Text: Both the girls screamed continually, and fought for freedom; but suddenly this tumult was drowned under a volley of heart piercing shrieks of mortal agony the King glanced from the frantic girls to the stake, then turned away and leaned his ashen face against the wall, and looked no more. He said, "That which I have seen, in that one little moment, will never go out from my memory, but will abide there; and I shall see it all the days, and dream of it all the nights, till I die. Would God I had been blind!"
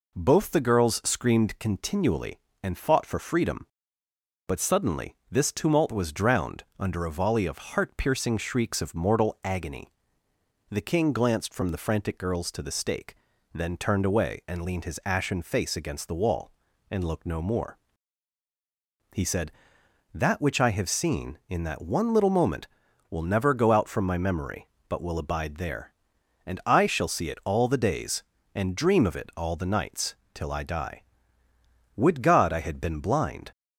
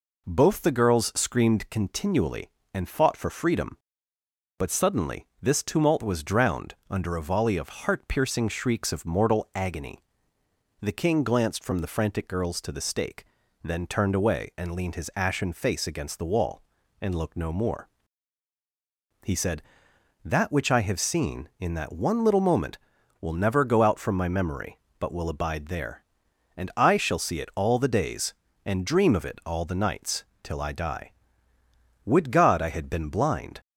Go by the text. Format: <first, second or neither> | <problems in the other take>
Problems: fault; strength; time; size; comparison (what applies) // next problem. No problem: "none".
neither | pauses between "suddenly" and "this"; slight; the same in both // pauses between "agony" and "the"; noticeable; the same in both